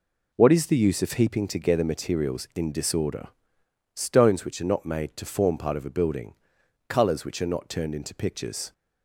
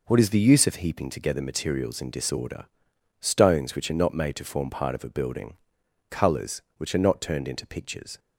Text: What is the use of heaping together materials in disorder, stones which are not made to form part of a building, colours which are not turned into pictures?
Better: neither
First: none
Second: none

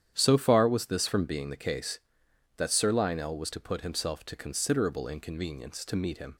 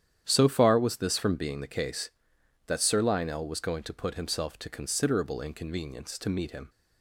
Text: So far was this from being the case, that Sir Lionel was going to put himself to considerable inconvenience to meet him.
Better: second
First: starts louder than the rest; strong; until 1.1 s; 10 dB // skips "going"; at 3.5 s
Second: starts louder than the rest; strong; until 1.2 s; 10 dB

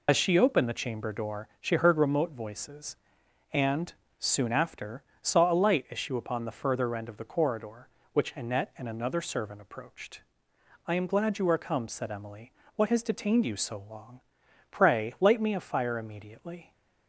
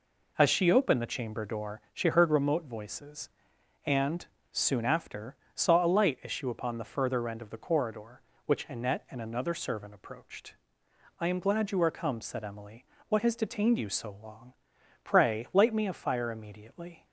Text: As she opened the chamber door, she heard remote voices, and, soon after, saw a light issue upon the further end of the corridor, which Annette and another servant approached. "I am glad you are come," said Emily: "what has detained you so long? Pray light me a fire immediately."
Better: second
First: loses the start of "As"; at 0.0 s; 45 ms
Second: none

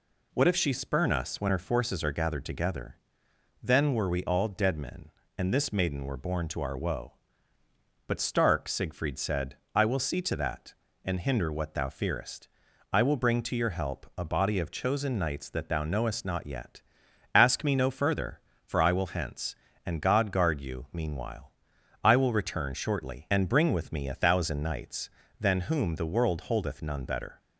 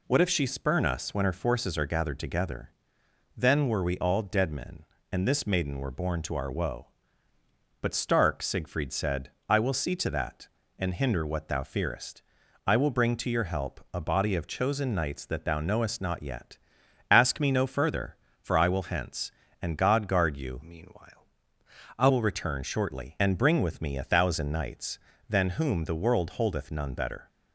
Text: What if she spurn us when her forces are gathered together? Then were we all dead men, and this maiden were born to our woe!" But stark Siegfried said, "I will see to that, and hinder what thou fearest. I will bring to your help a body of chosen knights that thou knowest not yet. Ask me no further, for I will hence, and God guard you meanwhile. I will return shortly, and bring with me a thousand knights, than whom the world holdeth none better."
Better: first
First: none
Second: changes voice from "meanwhile" to "I"; from 20.6 to 22.0 s; 1.4 s long

